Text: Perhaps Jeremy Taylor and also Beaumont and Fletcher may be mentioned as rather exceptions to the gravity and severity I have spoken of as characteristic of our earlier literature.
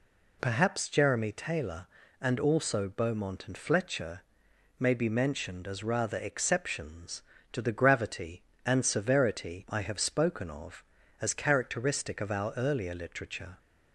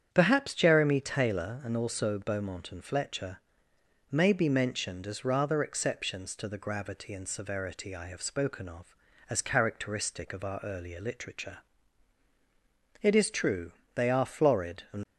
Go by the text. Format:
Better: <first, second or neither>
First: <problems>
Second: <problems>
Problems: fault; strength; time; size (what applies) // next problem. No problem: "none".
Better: first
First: pauses between "Fletcher" and "may"; noticeable; at 4.2 s; 0.58 s long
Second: starts louder than the rest; strong; until 1.1 s; 8.5 dB // pauses between "Fletcher" and "may"; noticeable; at 3.3 s; 0.72 s long // goes on to say "It is true they are florid and"; strong; from 13.0 s on; 2.0 s long